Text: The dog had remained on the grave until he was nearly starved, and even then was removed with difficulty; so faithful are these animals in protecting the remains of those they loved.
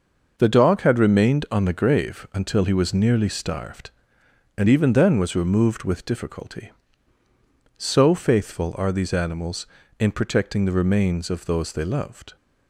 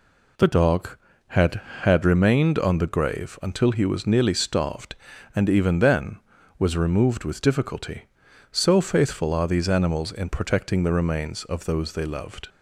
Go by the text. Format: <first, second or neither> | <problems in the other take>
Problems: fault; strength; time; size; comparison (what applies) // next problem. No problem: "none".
first | says "had" twice; at 1.8 s